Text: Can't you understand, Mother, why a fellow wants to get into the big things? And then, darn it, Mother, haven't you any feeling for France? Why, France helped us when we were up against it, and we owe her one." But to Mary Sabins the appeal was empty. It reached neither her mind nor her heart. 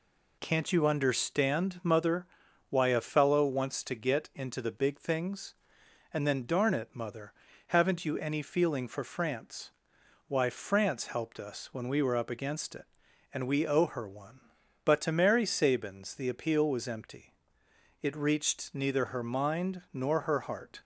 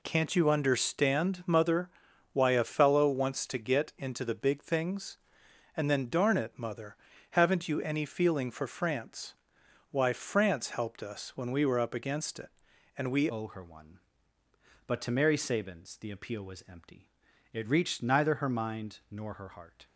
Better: first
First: none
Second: changes voice at "owe"; from 13.2 s on; 6.6 s long

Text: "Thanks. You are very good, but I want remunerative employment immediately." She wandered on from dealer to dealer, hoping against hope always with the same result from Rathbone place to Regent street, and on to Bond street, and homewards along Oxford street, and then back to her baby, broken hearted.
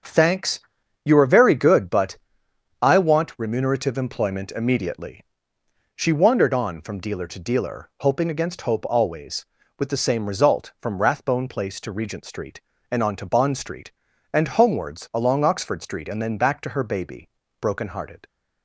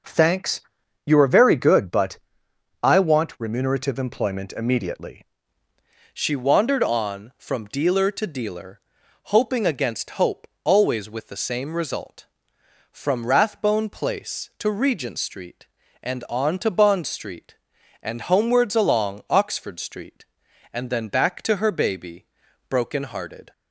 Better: first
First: starts louder than the rest; strong; until 1.5 s; 7.5 dB // pauses between "but" and "I"; noticeable; at 2.1 s; 0.64 s long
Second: starts louder than the rest; noticeable; until 1.5 s; 6 dB // pauses between "but" and "I"; noticeable; at 2.1 s; 0.64 s long // changes voice at "She"; from 6.1 s on; 17.4 s long // pauses between "hope" and "always"; slight; at 10.4 s; 0.16 s long

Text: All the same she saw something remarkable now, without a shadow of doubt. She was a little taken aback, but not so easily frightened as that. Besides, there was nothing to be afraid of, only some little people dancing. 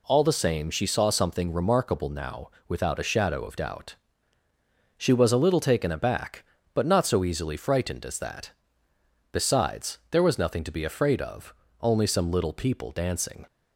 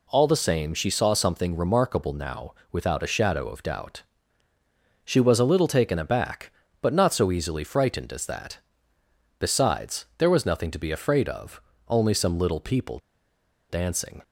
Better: first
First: none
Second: pauses between "people" and "dancing"; noticeable; at 12.9 s; 0.72 s long

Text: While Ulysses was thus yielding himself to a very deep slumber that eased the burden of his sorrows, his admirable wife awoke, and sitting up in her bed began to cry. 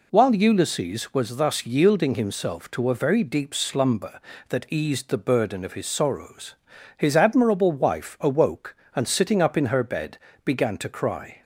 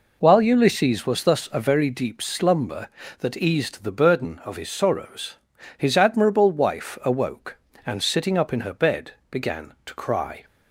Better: first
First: pauses between "bed" and "began"; slight; at 10.1 s; 0.24 s long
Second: skips "yielding himself to"; at 1.4 s // pauses between "bed" and "began"; slight; at 9.1 s; 0.18 s long

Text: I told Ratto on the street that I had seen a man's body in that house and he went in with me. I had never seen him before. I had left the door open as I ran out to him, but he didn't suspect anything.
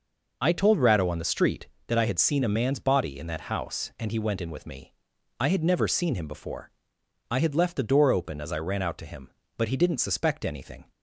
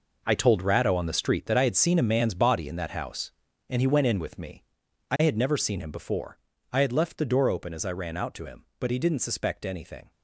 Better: first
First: none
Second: gets quieter; strong; throughout; 11.5 dB

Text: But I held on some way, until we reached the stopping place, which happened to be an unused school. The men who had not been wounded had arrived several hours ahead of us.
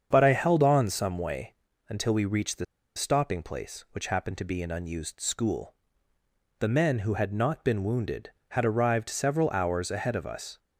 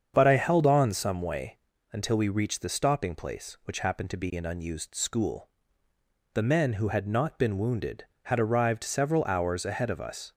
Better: second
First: starts louder than the rest; strong; until 1.1 s; 7.5 dB // pauses between "the" and "stopping"; slight; at 2.6 s; 0.31 s long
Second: starts louder than the rest; strong; until 1.1 s; 7.5 dB

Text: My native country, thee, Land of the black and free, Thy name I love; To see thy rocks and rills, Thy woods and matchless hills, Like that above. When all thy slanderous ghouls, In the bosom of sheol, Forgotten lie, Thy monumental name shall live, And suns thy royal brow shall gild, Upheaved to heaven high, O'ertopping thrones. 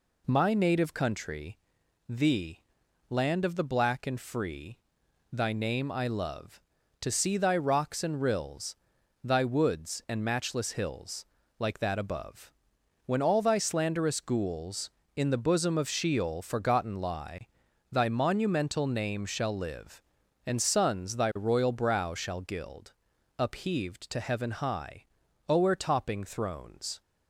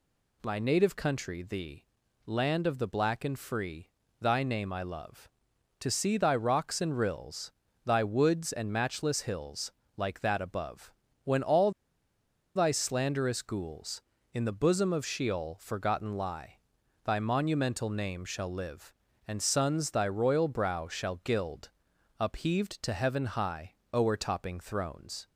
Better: first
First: none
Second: pauses between "all" and "thy"; noticeable; at 11.7 s; 0.83 s long

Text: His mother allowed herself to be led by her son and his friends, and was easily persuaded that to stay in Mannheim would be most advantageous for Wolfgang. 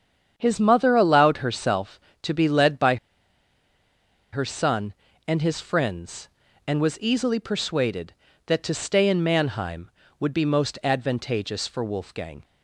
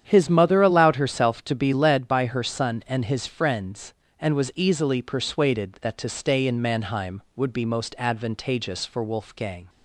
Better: second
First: starts louder than the rest; strong; until 1.3 s; 8 dB // pauses between "by" and "her"; strong; at 2.9 s; 1.3 s long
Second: starts louder than the rest; strong; until 1.0 s; 9 dB

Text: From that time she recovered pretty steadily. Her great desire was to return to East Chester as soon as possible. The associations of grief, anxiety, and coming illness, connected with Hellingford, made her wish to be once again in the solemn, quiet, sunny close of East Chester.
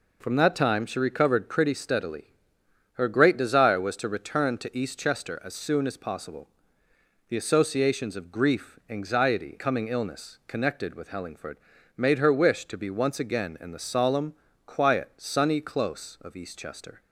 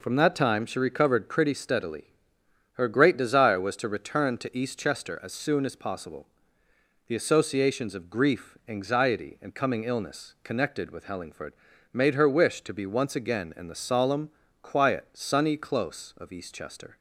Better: second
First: skips "and"; at 9.5 s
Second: none

